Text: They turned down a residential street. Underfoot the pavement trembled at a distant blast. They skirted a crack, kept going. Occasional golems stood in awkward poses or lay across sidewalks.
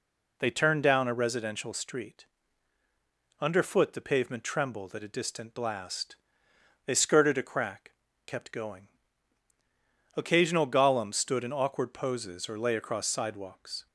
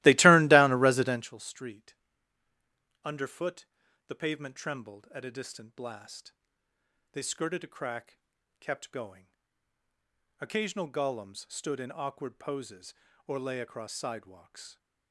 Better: first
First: none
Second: starts louder than the rest; strong; until 1.3 s; 17.5 dB // pauses between "Underfoot" and "the"; at 3.6 s; 0.42 s long

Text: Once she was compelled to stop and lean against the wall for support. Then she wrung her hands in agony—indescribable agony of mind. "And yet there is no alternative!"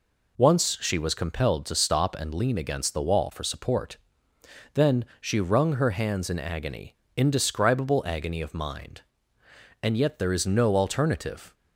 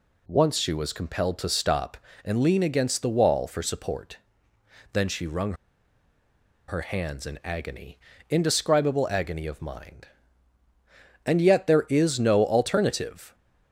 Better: first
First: none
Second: pauses between "wrung" and "her"; at 5.5 s; 1.1 s long

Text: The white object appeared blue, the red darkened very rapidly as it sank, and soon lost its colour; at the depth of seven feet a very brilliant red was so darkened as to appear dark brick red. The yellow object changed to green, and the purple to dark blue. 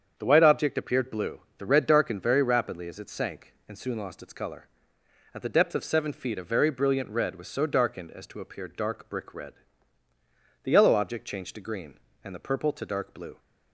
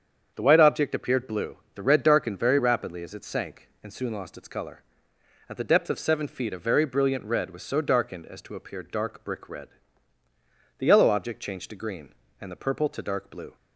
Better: neither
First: starts louder than the rest; strong; until 1.1 s; 7.5 dB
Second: starts louder than the rest; strong; until 1.3 s; 7.5 dB

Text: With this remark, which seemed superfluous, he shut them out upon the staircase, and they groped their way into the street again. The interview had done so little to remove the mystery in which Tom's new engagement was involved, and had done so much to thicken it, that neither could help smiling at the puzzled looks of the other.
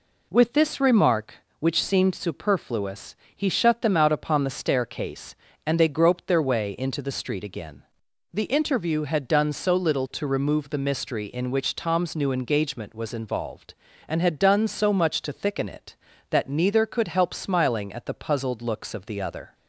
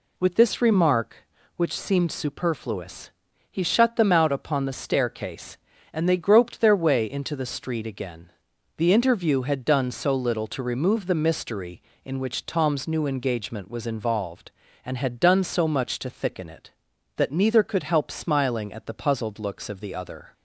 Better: neither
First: none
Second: none

